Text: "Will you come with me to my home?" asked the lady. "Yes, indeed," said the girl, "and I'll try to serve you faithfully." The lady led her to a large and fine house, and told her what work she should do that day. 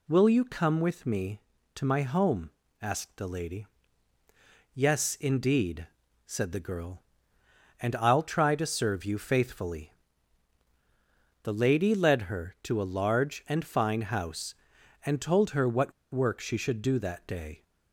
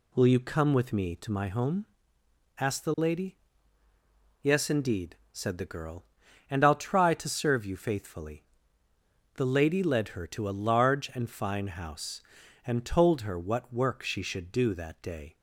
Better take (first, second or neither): second